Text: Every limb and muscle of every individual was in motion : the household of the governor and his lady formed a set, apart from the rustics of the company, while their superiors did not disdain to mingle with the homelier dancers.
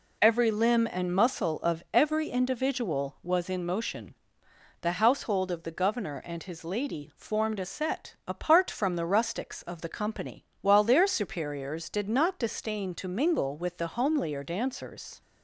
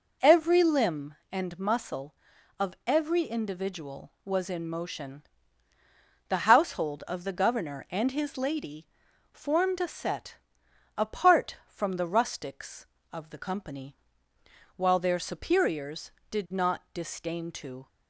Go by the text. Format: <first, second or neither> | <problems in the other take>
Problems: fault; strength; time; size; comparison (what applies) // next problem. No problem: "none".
first | pauses between "lady" and "formed"; noticeable; at 8.8 s; 0.46 s long // stops before "mingle with the homelier dancers"; at 17.8 s